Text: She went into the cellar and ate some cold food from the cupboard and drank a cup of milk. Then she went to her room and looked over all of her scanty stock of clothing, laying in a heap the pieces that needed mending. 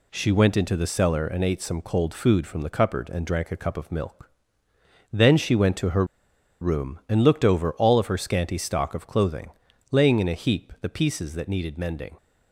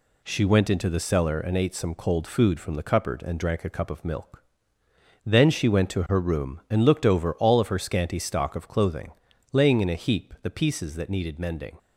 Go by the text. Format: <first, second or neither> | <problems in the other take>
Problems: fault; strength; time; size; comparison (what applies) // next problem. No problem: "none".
second | pauses between "her" and "room"; noticeable; at 6.0 s; 0.56 s long